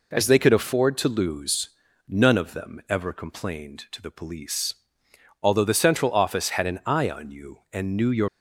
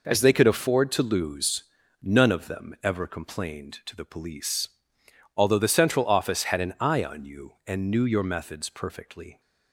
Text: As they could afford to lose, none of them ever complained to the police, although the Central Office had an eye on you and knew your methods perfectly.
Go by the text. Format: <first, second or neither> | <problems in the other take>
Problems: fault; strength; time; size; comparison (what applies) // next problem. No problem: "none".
second | stops before "methods perfectly"; at 8.2 s